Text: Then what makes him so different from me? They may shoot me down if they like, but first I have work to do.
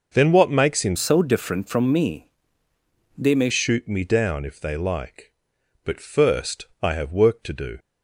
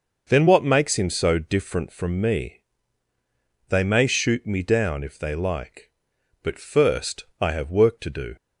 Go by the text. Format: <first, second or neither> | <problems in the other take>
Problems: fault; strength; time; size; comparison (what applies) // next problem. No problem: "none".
second | changes voice from "so" to "may"; from 0.9 to 3.4 s; 2.5 s long